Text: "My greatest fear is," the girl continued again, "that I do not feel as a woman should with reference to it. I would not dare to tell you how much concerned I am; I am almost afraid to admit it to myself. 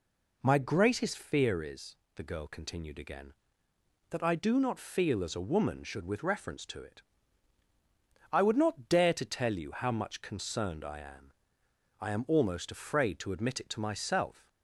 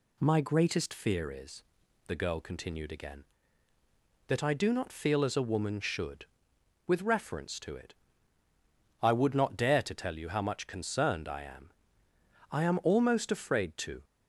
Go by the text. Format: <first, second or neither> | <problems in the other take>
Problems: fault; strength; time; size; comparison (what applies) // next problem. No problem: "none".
first | stops before "admit it to myself"; at 14.0 s